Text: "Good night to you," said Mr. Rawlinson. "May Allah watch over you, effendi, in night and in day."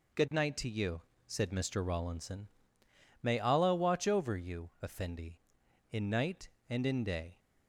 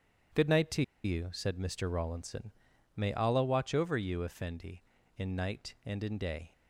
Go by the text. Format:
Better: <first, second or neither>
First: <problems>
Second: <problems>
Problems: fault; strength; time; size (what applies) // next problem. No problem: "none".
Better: first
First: none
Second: starts louder than the rest; strong; until 1.5 s; 9 dB // pauses between "to" and "you"; slight; at 0.8 s; 0.21 s long